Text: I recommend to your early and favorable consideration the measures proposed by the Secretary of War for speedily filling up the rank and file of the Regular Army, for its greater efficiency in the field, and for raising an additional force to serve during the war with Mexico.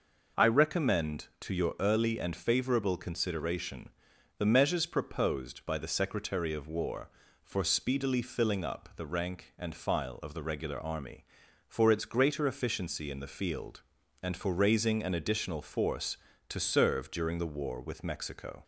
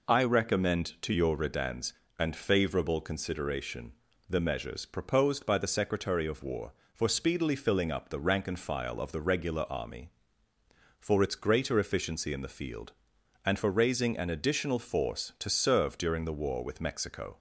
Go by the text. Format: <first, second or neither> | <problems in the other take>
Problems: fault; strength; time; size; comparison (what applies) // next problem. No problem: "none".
first | says "redans" for "early"; at 1.3 s // pauses between "consideration" and "the"; slight; at 3.9 s; 0.36 s long; noticeable in the first